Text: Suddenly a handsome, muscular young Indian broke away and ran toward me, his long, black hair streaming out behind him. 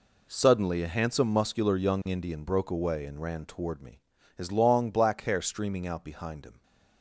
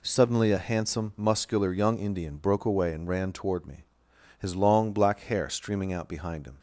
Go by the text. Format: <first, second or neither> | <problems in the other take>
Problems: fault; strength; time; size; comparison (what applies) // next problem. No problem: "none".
neither | none